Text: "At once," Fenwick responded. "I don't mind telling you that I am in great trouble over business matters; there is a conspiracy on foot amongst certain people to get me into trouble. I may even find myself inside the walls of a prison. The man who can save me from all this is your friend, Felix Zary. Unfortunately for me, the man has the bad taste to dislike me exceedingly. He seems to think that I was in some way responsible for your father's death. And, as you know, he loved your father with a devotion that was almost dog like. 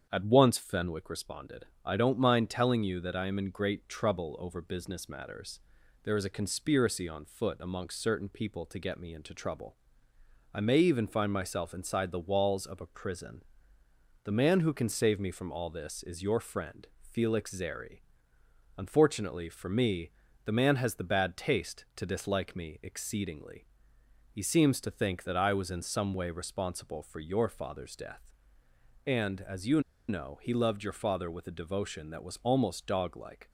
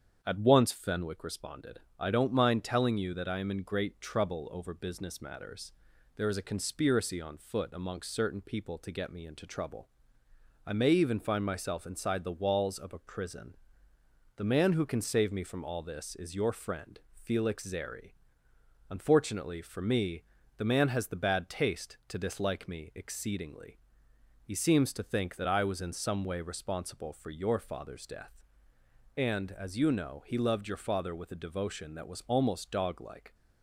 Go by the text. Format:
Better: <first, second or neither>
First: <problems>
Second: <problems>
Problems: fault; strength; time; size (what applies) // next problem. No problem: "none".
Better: second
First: starts louder than the rest; strong; until 1.1 s; 8 dB // pauses between "you" and "know"; slight; at 29.7 s; 0.28 s long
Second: starts louder than the rest; strong; until 1.2 s; 8 dB